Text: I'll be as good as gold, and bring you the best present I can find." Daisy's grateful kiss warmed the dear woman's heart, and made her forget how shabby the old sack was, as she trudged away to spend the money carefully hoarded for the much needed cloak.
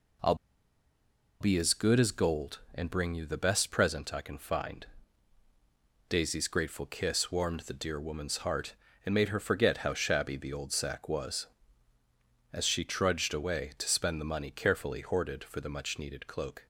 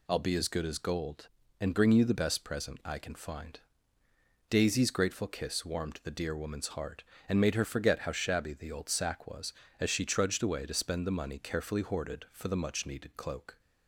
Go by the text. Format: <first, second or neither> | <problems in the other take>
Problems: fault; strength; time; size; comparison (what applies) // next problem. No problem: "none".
second | pauses between "I'll" and "be"; at 0.3 s; 1.0 s long